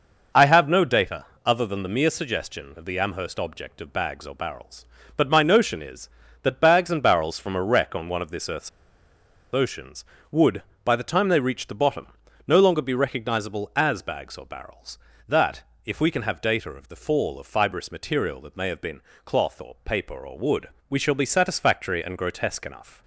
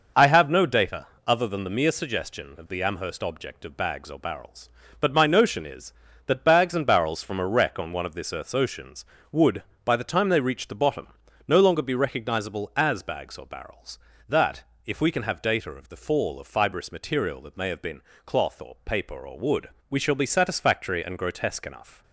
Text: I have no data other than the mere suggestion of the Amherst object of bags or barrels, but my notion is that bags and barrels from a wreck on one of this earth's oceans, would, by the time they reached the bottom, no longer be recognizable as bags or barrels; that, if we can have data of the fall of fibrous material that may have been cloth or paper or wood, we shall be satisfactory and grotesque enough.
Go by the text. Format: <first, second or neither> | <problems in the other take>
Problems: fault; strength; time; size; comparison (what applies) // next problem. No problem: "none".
second | pauses between "data" and "other"; slight; at 1.2 s; 0.18 s long; slight in the second // pauses between "earth's" and "oceans"; noticeable; at 8.6 s; 0.84 s long // pauses between "been" and "cloth"; slight; at 19.0 s; 0.24 s long; slight in the second